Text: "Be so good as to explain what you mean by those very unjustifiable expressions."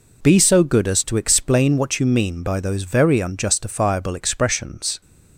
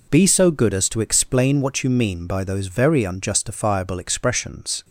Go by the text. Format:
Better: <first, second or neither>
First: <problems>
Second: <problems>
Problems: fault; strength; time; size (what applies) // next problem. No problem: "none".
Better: neither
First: none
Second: none